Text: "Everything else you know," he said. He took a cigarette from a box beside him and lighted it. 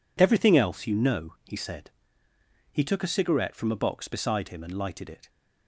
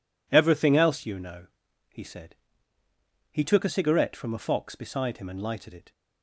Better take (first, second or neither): first